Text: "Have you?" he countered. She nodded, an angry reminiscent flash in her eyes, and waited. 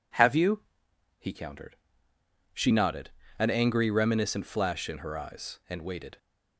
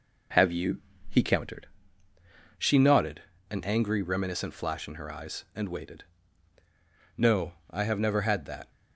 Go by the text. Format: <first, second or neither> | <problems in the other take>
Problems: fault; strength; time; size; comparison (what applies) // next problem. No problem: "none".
first | goes on to say "No I have never had that"; from 7.1 s on; 1.5 s long